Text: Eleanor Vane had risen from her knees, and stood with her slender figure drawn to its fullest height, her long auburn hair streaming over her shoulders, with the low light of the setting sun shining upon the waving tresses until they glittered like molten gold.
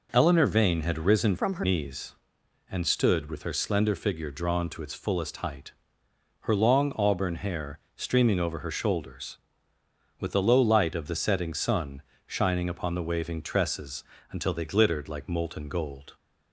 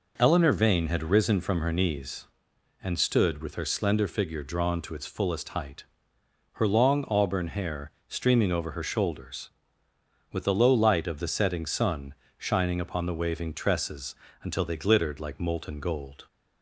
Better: second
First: changes voice from "from" to "her"; from 1.3 to 1.6 s; 0.3 s long // pauses between "hair" and "streaming"; slight; at 7.7 s; 0.16 s long // pauses between "sun" and "shining"; slight; at 12.0 s; 0.26 s long // pauses between "tresses" and "until"; slight; at 14.0 s; 0.26 s long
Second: pauses between "hair" and "streaming"; slight; at 7.9 s; 0.16 s long // pauses between "sun" and "shining"; slight; at 12.1 s; 0.25 s long // pauses between "tresses" and "until"; slight; at 14.1 s; 0.26 s long

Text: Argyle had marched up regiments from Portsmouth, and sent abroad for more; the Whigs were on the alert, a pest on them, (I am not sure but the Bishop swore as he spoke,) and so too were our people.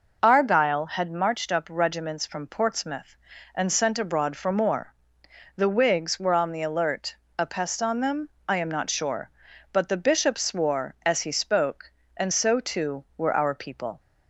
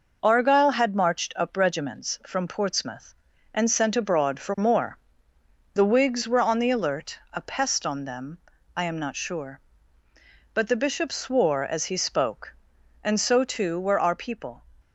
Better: neither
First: none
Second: none

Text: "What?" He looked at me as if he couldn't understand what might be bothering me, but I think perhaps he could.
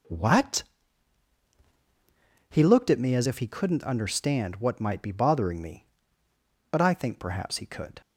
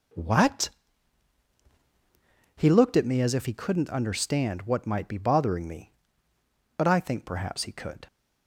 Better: neither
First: none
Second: none

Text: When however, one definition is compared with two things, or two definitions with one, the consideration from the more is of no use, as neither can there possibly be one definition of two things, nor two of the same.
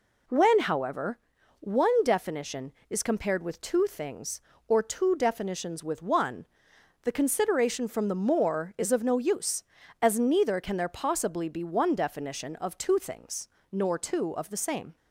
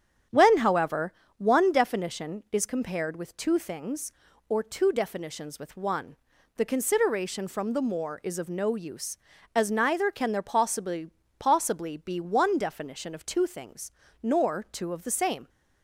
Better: first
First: none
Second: starts louder than the rest; strong; until 1.5 s; 9.5 dB // says "possibly" twice; at 11.3 s

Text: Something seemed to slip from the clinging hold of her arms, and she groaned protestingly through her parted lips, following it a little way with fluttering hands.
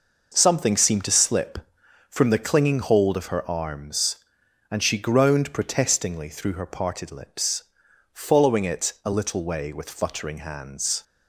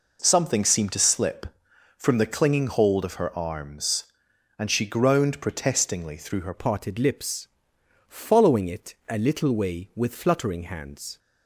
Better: first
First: none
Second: changes voice at "parted"; from 6.5 s on; 4.6 s long

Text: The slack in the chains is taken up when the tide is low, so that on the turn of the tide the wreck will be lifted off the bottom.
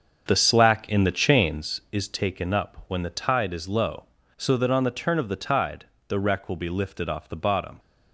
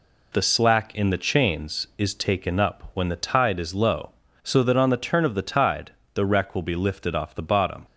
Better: second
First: starts louder than the rest; until 1.8 s; 6.5 dB // pauses between "tide" and "the"; slight; at 5.8 s; 0.24 s long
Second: pauses between "tide" and "the"; slight; at 5.9 s; 0.24 s long

